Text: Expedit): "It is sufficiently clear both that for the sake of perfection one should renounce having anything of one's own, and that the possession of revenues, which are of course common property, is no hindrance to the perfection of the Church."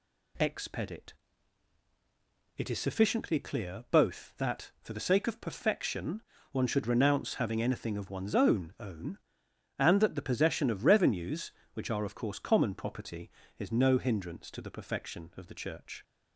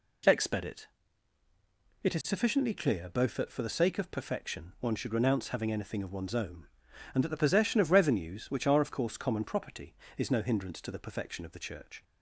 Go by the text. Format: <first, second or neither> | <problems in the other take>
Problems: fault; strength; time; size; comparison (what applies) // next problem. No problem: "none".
second | pauses between "perfection" and "one"; slight; at 6.2 s; 0.30 s long // says "own" twice; at 8.7 s